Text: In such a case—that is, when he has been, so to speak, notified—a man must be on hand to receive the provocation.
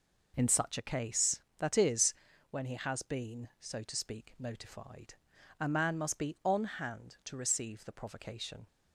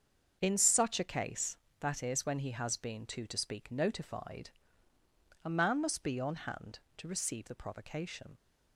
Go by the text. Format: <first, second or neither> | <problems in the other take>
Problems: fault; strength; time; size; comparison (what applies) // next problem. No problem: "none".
first | starts louder than the rest; until 1.4 s; 7 dB // says "too" for "so"; at 3.0 s